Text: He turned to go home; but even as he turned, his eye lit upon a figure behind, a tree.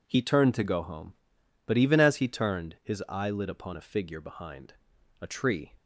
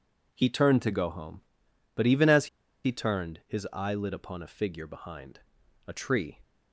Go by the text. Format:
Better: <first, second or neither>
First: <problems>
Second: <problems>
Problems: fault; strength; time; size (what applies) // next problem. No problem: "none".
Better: first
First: none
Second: pauses between "as" and "he"; at 2.4 s; 0.37 s long